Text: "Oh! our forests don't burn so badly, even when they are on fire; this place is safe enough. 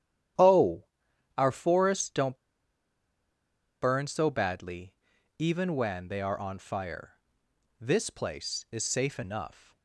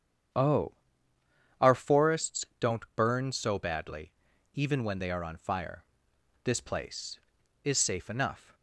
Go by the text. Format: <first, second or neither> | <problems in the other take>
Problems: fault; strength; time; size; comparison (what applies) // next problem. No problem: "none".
second | starts louder than the rest; strong; until 1.9 s; 10.5 dB; strong in the second // pauses between "don't" and "burn"; strong; at 2.3 s; 1.4 s long